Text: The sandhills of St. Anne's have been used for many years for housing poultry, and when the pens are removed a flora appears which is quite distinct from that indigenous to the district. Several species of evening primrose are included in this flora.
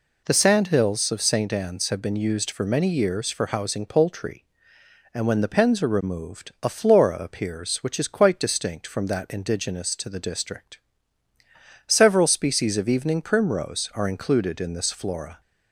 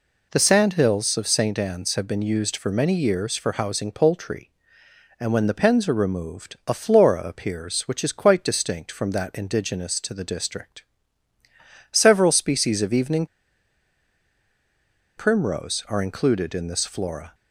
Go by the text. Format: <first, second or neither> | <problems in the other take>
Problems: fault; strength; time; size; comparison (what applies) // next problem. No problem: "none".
first | pauses between "evening" and "primrose"; strong; at 13.2 s; 1.9 s long